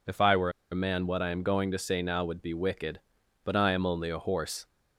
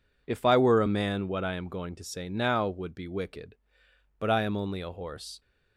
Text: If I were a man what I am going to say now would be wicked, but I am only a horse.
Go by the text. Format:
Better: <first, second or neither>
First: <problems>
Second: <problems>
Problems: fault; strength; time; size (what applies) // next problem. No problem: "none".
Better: second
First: pauses between "were" and "a"; slight; at 0.5 s; 0.20 s long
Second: none